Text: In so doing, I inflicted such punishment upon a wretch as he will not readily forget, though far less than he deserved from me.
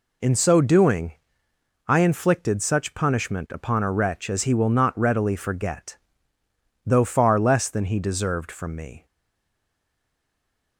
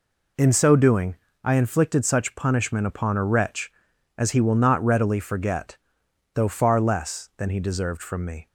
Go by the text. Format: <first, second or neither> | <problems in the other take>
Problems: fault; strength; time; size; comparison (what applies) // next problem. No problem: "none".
second | stays silent after the last word; noticeable; from 9.0 s on; 1.7 s long